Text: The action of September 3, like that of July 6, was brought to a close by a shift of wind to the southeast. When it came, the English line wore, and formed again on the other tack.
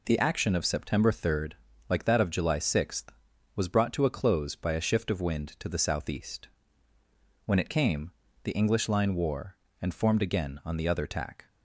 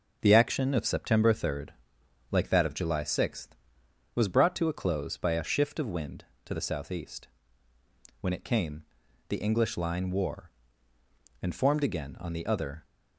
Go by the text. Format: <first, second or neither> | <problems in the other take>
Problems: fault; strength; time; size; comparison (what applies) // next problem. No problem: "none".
first | stops before "tack"; at 12.8 s